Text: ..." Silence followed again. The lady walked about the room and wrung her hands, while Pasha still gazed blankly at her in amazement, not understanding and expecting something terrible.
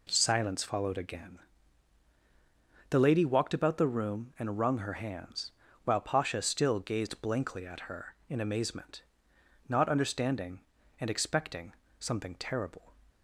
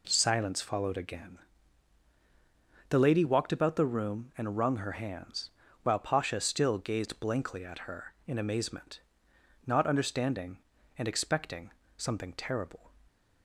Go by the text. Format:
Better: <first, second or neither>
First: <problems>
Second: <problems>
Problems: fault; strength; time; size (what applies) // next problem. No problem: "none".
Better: neither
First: pauses between "expecting" and "something"; slight; at 11.7 s; 0.24 s long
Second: pauses between "expecting" and "something"; slight; at 11.7 s; 0.24 s long